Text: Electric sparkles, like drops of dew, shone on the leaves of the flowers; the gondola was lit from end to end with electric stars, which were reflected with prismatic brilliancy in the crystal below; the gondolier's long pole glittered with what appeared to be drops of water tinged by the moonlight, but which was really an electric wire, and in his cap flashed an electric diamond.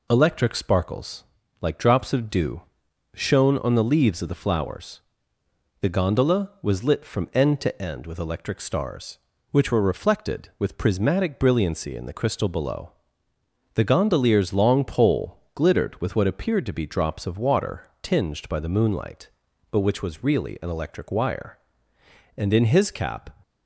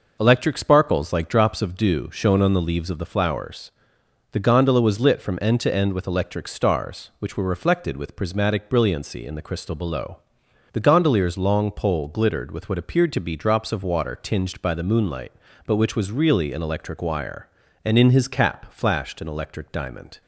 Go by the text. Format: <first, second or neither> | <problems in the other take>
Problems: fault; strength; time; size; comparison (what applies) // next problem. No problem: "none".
second | stops before "flashed an electric diamond"; at 23.4 s